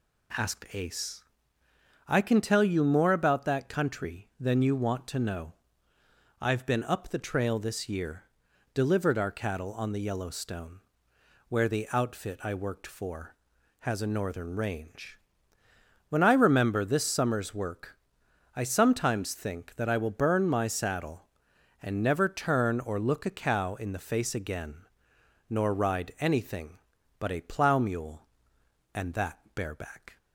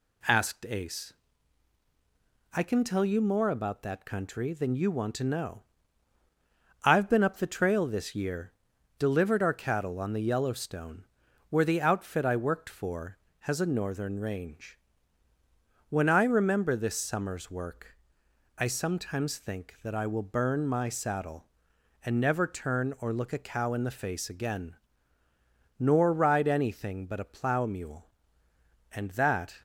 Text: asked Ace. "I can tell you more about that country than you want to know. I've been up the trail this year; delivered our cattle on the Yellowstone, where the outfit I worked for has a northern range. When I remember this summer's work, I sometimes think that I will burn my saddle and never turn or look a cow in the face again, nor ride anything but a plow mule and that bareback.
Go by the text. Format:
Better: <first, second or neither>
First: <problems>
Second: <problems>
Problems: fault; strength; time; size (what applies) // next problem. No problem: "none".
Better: first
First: none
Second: stops before "bareback"; at 29.5 s